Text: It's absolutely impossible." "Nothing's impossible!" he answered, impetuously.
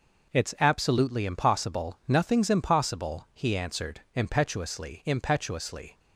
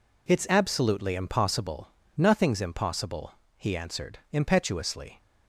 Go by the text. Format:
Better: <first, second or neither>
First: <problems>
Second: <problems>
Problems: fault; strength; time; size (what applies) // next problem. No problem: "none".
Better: second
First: says "impetuously" twice; at 5.0 s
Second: none